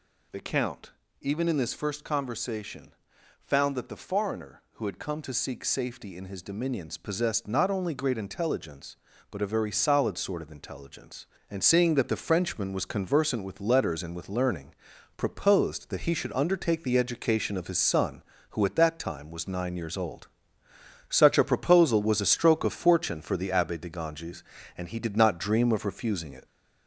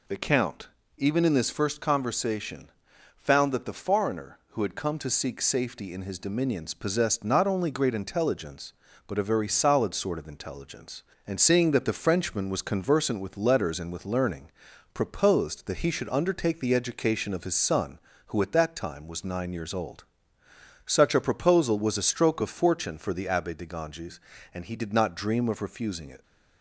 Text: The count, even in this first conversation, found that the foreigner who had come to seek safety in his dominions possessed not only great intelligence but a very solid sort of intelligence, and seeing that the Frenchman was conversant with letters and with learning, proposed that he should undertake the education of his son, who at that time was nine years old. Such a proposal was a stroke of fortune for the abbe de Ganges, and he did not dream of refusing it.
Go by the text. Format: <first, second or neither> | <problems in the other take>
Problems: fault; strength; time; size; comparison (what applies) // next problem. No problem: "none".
second | gets louder; noticeable; throughout; 4 dB